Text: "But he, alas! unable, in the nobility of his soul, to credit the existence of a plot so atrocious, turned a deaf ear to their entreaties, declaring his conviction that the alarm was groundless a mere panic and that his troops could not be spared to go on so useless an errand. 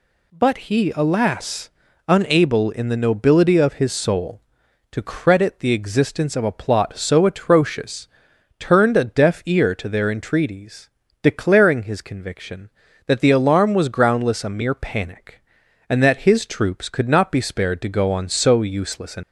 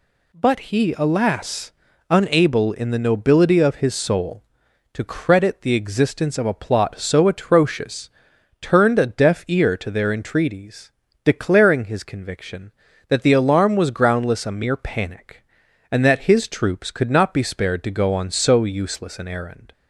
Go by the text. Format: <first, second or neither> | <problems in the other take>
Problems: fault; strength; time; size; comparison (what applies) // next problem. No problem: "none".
second | stops before "errand"; at 19.2 s